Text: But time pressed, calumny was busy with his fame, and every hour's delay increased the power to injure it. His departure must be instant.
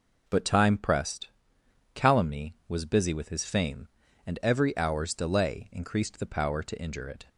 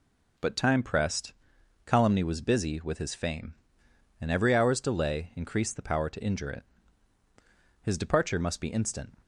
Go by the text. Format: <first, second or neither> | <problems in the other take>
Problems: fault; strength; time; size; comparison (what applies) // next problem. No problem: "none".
second | stops before "His departure must be instant"; at 7.2 s